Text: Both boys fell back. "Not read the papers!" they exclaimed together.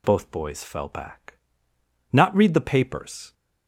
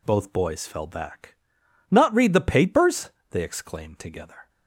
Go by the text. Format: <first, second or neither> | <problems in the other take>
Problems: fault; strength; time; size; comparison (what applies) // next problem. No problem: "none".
second | stops before "they exclaimed together"; at 3.3 s